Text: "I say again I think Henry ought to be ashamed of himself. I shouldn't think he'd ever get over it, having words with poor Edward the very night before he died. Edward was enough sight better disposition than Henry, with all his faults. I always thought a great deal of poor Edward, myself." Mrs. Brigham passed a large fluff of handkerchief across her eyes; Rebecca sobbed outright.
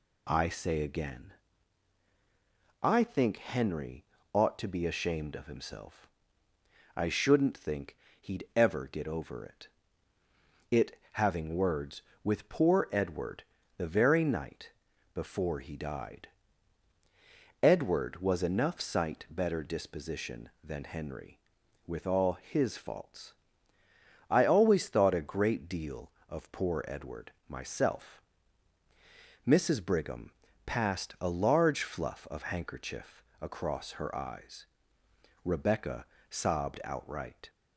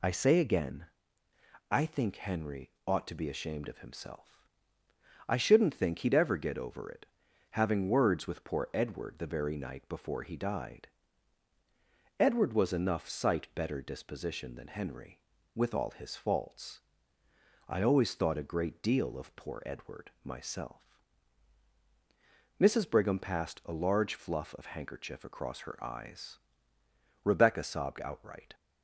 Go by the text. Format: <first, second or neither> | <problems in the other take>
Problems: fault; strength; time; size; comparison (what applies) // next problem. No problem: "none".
second | pauses between "again" and "I"; strong; at 1.3 s; 1.5 s long; noticeable in the second // pauses between "Henry" and "ought"; slight; at 4.0 s; 0.30 s long; slight in the second // pauses between "think" and "he'd"; slight; at 7.9 s; 0.24 s long // says "it" twice; at 10.6 s // pauses between "Edward" and "the"; slight; at 13.4 s; 0.34 s long // pauses between "night" and "before"; at 14.6 s; 0.44 s long // pauses between "Brigham" and "passed"; slight; at 30.3 s; 0.34 s long // pauses between "handkerchief" and "across"; slight; at 33.2 s; 0.16 s long // pauses between "Rebecca" and "sobbed"; slight; at 36.0 s; 0.24 s long